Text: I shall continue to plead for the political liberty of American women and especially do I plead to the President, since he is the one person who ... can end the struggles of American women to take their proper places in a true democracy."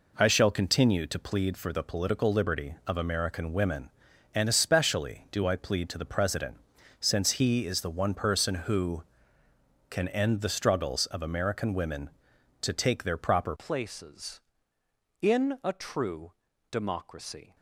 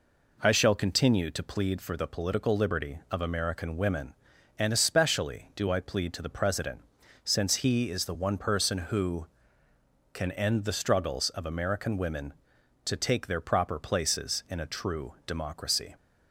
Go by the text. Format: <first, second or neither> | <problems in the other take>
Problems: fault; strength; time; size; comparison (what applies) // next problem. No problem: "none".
second | changes voice at "places"; from 13.5 s on; 4.0 s long // pauses between "true" and "democracy"; slight; at 16.3 s; 0.36 s long